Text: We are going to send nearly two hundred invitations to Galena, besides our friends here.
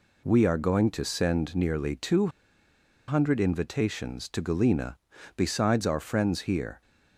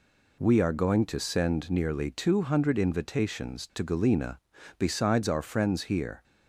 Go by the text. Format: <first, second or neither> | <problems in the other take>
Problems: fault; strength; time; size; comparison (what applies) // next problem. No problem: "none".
second | pauses between "two" and "hundred"; noticeable; at 2.2 s; 0.79 s long